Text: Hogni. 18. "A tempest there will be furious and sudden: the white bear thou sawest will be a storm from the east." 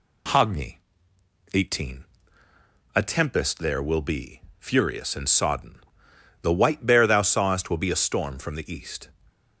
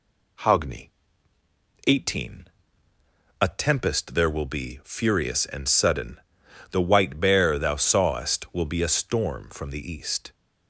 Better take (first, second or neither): second